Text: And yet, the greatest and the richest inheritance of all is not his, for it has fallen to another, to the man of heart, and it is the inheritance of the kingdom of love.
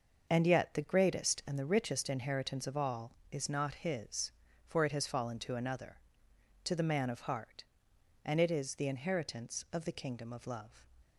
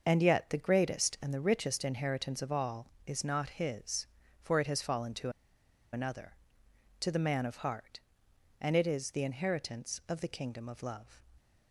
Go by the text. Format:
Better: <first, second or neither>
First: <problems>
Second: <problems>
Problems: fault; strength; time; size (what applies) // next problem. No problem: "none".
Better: first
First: starts louder than the rest; until 1.3 s; 6.5 dB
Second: starts louder than the rest; until 1.0 s; 6 dB // pauses between "to" and "another"; noticeable; at 5.2 s; 0.63 s long